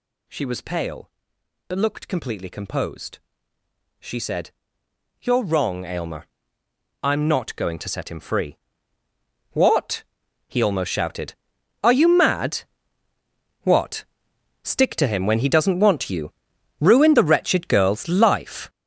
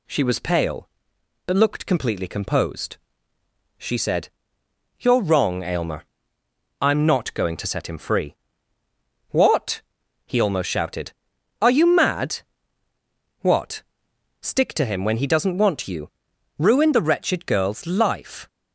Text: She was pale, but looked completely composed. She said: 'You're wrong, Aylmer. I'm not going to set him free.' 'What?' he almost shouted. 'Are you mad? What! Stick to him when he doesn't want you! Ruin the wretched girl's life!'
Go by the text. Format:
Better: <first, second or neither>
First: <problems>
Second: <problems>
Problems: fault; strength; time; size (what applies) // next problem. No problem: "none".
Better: second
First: gets louder; strong; throughout; 10 dB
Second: none